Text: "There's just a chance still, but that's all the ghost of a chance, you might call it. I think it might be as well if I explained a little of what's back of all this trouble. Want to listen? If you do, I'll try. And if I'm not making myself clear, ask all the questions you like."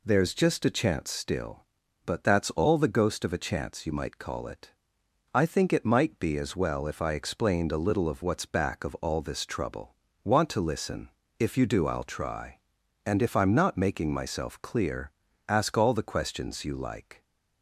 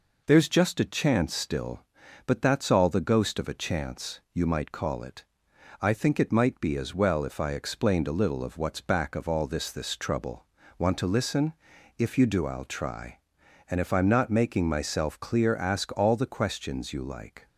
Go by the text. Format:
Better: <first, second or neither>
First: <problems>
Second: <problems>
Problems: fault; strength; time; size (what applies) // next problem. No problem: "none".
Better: first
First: none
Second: says "this" twice; at 9.6 s